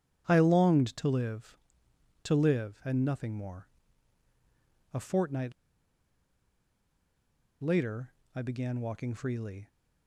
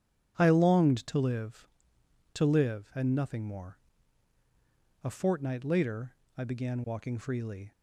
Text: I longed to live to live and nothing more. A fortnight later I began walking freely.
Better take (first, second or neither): second